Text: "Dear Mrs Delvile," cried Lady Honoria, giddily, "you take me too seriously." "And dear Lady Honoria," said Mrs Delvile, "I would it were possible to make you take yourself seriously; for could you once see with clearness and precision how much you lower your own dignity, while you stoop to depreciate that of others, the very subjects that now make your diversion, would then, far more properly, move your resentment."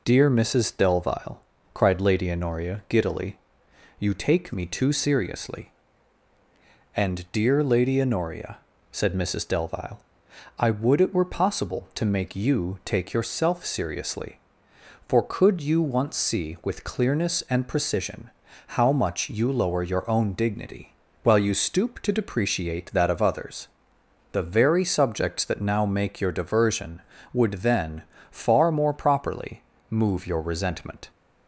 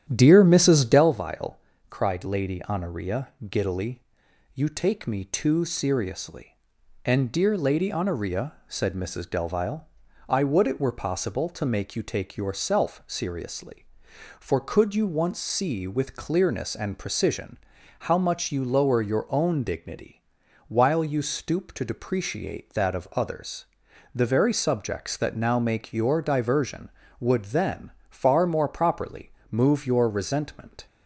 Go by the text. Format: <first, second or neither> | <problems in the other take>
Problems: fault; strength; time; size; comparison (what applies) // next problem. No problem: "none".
first | starts louder than the rest; strong; until 1.2 s; 10.5 dB // pauses between "precision" and "how"; at 17.5 s; 0.42 s long; also in the first